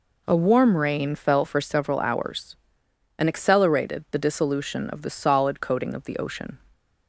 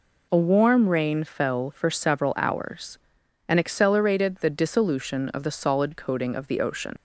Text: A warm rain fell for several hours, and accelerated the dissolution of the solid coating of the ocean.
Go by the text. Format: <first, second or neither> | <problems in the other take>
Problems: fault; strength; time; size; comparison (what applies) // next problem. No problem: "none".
first | leaves "ocean" unfinished; at 6.9 s; 100 ms